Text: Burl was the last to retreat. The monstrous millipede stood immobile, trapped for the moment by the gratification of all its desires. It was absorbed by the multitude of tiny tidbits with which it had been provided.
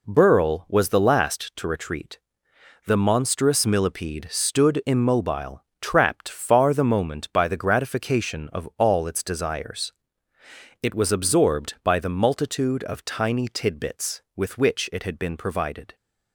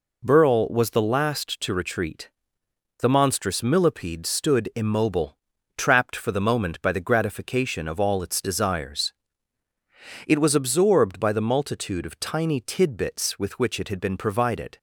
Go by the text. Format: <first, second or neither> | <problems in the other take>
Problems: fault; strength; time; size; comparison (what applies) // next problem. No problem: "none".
second | says "far" for "for"; at 6.2 s